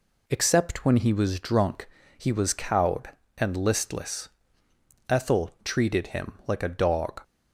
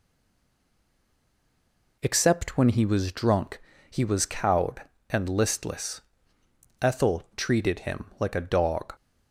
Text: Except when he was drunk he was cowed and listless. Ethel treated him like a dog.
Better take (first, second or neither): first